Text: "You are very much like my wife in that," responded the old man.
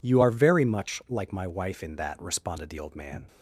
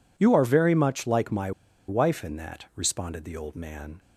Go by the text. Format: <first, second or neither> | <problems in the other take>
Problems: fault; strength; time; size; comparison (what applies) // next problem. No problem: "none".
first | pauses between "my" and "wife"; at 1.5 s; 0.37 s long